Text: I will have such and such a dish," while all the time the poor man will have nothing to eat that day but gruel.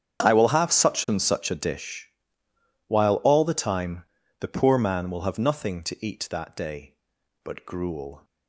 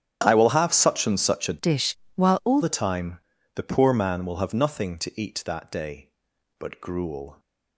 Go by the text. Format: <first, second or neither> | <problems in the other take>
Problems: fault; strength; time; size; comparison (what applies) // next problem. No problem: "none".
first | starts louder than the rest; strong; until 1.2 s; 9.5 dB; strong in the first // changes voice from "dish" to "all"; from 1.5 to 2.5 s; 1.0 s long // pauses between "time" and "the"; slight; at 3.1 s; 0.36 s long; slight in the first